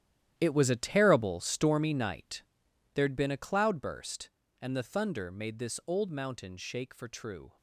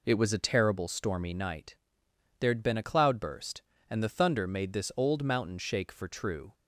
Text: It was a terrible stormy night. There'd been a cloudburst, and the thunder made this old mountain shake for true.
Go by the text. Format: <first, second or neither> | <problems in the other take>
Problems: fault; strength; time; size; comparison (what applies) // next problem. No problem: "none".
second | gets quieter; strong; throughout; 12.5 dB